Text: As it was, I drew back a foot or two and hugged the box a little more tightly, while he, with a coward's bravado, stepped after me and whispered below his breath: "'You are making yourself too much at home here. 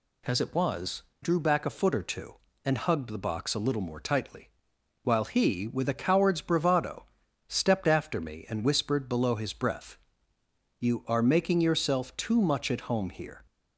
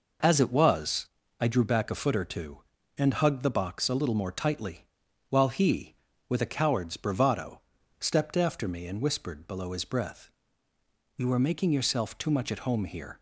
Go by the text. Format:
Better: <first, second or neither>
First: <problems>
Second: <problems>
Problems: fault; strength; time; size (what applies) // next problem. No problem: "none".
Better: second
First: skips "I"; at 1.1 s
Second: none